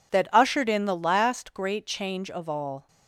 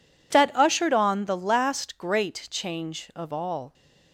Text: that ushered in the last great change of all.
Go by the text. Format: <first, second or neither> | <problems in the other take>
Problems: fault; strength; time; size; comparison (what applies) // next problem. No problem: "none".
first | says "on" for "in"; at 0.9 s